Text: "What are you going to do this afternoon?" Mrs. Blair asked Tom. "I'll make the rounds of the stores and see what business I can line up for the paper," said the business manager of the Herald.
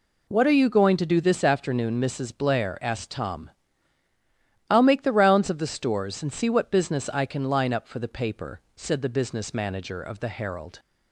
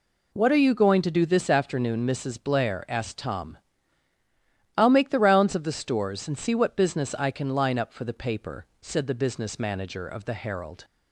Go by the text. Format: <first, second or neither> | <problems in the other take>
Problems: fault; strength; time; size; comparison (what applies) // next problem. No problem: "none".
neither | none